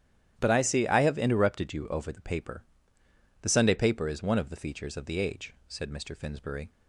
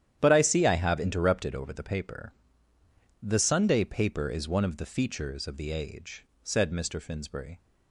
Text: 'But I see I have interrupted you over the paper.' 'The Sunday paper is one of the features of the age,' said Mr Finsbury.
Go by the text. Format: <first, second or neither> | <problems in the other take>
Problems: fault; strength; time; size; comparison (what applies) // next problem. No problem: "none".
first | starts louder than the rest; strong; until 1.2 s; 10.5 dB; strong in the first // skips "you"; at 1.5 s